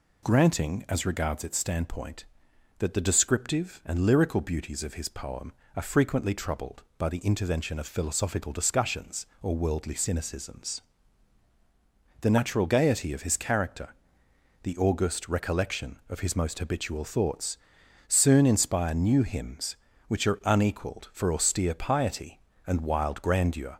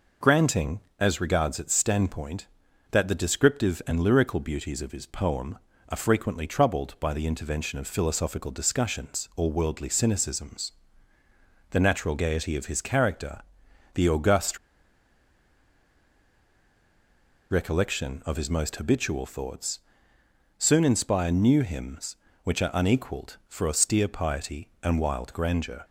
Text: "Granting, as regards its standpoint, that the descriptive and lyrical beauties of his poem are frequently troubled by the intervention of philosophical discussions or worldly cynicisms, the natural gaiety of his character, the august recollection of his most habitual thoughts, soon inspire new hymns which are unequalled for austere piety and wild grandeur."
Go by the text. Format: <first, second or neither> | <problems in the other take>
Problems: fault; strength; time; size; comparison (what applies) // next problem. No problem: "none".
first | pauses between "august" and "recollection"; strong; at 14.5 s; 2.9 s long